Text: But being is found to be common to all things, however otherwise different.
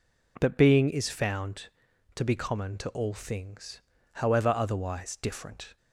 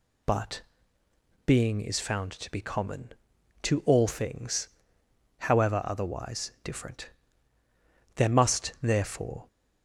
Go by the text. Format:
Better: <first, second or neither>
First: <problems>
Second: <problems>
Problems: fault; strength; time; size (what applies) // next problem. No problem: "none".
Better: first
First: none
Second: pauses between "But" and "being"; noticeable; at 0.6 s; 0.84 s long // goes on to say "There must therefore"; from 8.1 s on; 1.3 s long